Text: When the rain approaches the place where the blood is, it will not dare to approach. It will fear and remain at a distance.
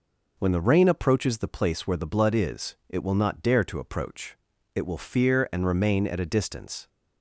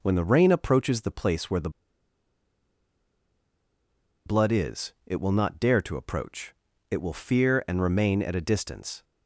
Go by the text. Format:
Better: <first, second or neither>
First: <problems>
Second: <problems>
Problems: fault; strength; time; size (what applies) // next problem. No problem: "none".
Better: first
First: none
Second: pauses between "the" and "blood"; strong; at 1.6 s; 2.5 s long